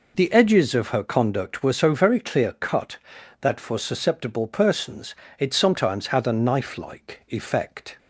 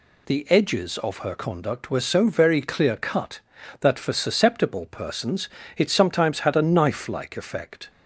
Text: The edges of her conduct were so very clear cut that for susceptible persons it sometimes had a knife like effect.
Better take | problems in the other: neither | pauses between "persons" and "it"; slight; the same in both

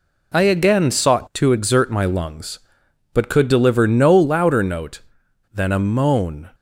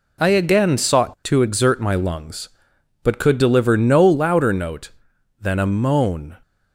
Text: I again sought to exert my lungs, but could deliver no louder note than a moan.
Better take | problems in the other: neither | none

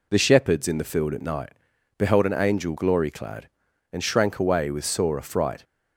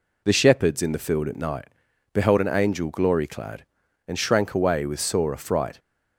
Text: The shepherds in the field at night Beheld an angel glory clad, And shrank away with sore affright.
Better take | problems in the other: neither | pauses between "night" and "Beheld"; the same in both

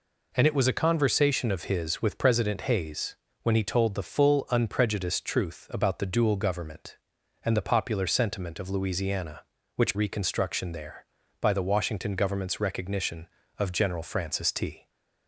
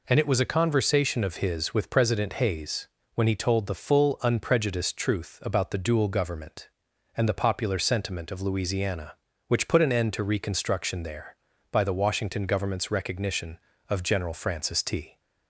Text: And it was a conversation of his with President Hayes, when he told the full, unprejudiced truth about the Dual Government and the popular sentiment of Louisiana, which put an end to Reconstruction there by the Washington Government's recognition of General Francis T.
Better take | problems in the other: second | skips "put an end to"; at 9.9 s

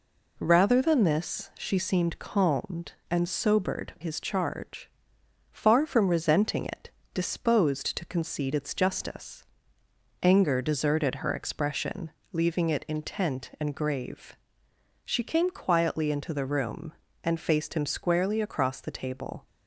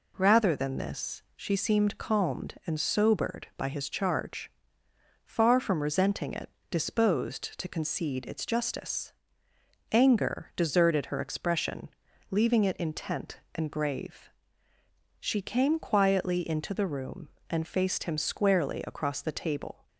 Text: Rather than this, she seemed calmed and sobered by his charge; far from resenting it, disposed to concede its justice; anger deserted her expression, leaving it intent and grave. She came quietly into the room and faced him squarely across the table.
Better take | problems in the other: second | skips "by"; at 3.9 s

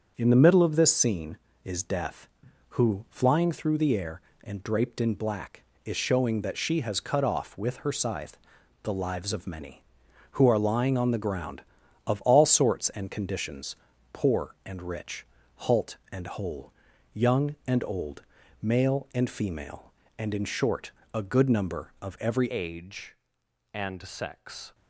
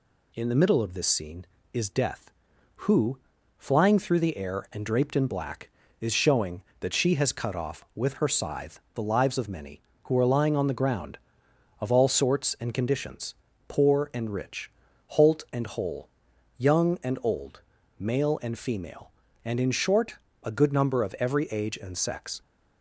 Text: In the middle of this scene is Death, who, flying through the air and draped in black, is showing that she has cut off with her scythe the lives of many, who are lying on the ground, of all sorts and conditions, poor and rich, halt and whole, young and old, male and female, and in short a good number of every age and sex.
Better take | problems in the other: second | starts louder than the rest; strong; until 1.1 s; 7.5 dB // pauses between "scythe" and "the"; noticeable; at 8.3 s; 0.46 s long; slight in the second // pauses between "short" and "a"; slight; at 20.9 s; 0.20 s long; slight in the second // changes voice at "age"; from 22.5 s on; 2.2 s long

